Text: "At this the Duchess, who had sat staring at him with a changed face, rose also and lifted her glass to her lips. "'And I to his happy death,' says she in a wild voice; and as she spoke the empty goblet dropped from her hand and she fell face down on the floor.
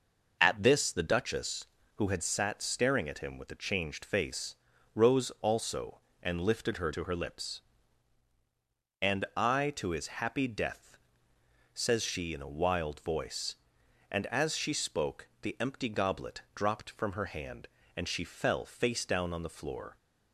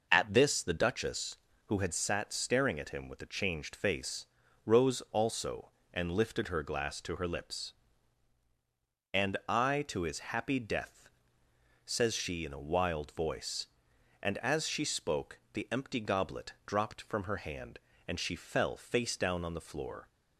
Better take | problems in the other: second | skips "glass"; at 6.9 s

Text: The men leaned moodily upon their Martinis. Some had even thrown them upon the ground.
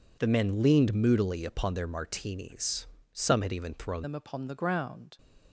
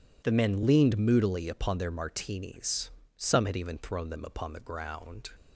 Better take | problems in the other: second | changes voice at "them"; from 4.0 s on; 1.1 s long

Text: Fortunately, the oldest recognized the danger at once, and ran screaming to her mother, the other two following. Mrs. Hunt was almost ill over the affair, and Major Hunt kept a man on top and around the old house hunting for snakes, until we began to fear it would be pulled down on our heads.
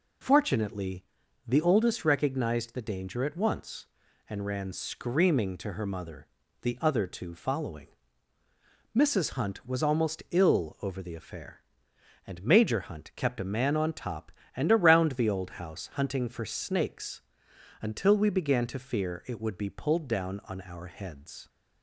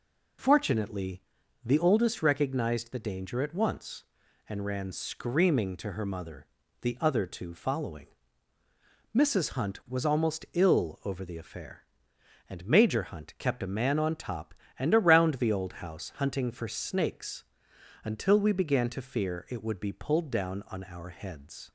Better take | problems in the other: neither | none

